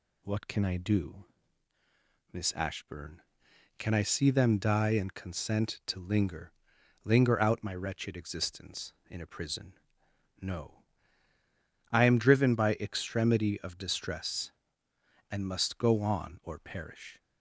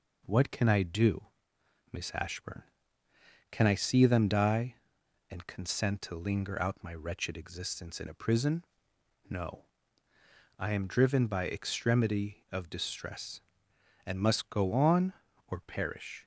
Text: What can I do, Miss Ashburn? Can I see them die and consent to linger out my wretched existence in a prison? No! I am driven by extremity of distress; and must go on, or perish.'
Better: second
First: says "linger" twice; at 7.0 s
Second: none

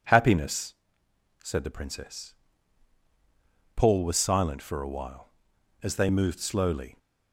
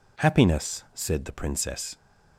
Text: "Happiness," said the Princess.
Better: second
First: goes on to say "Paul was silent for a while as they moved slowly"; strong; from 3.7 s on; 3.2 s long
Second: none

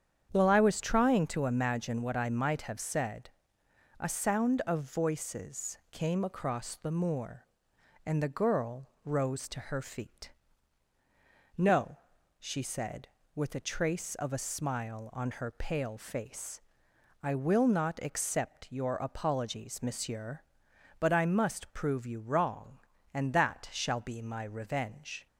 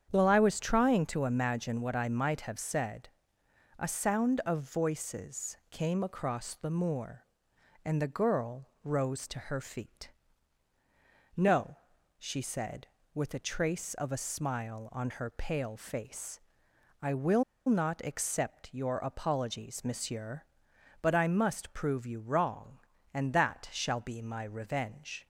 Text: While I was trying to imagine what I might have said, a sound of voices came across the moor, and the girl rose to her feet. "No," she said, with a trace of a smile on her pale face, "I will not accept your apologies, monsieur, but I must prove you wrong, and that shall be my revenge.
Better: first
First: starts louder than the rest; strong; until 1.3 s; 8 dB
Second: starts louder than the rest; strong; until 1.1 s; 8 dB // pauses between "will" and "not"; slight; at 17.4 s; 0.25 s long

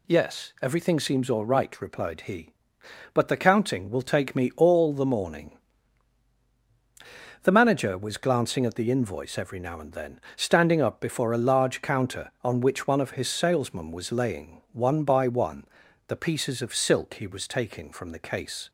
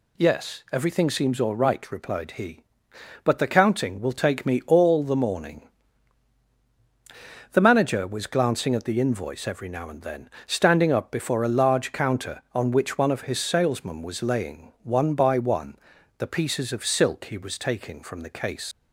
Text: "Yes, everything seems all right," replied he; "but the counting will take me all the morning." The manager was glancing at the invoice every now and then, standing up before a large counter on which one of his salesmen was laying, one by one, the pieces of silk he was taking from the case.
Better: first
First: none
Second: leaves "case" unfinished; at 18.7 s; 90 ms

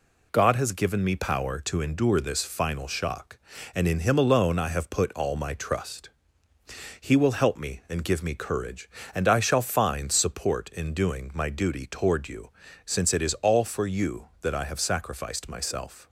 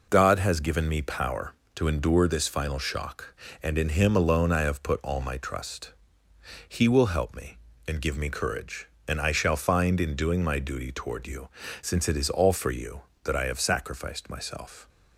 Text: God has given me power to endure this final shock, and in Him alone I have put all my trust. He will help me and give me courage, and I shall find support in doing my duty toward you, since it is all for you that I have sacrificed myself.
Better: first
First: none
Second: skips "support"; at 10.0 s

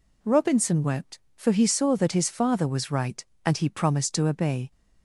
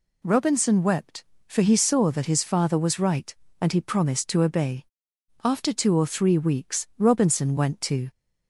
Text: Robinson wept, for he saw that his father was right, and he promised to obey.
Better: first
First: none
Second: goes on to say "After two or three weeks Robinson went to"; strong; from 5.4 s on; 2.6 s long

